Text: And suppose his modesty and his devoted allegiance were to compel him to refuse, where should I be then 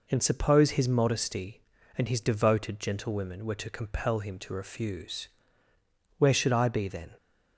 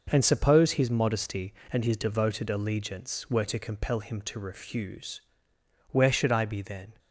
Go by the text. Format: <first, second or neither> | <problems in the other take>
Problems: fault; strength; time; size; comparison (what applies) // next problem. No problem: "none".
second | says "gentlewomen" for "allegiance"; at 2.7 s